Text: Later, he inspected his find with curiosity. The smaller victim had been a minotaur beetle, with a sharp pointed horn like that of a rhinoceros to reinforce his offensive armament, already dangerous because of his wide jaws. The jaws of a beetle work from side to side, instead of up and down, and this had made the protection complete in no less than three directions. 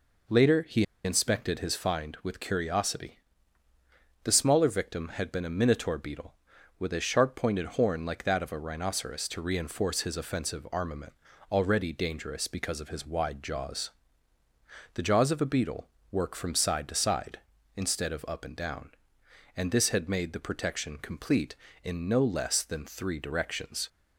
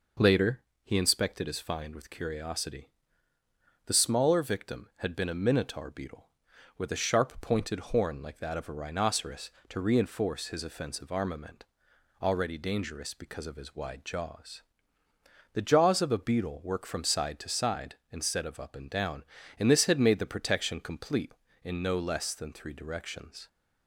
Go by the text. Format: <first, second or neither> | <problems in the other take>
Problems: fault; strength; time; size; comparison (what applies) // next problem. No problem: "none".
second | pauses between "he" and "inspected"; slight; at 0.8 s; 0.20 s long // pauses between "beetle" and "work"; slight; at 15.8 s; 0.24 s long